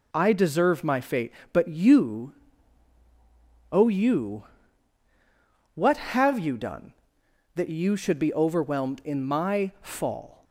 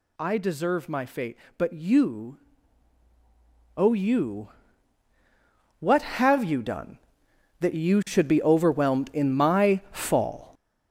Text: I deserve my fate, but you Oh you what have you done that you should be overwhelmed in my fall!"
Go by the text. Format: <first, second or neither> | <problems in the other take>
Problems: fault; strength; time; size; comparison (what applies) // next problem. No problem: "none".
first | gets louder; throughout; 6.5 dB // pauses between "you" and "Oh"; strong; at 2.3 s; 1.3 s long; strong in the first // pauses between "you" and "what"; strong; at 4.4 s; 1.3 s long; strong in the first